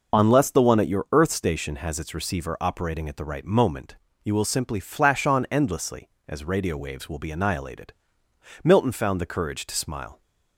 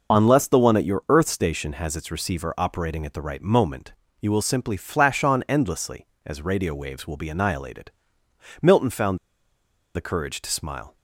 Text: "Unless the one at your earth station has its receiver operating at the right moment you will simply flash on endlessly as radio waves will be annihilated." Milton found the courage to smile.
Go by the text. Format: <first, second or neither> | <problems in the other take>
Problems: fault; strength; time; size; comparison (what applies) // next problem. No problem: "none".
first | pauses between "moment" and "you"; slight; at 3.9 s; 0.26 s long; slight in the first // pauses between "found" and "the"; noticeable; at 9.1 s; 0.77 s long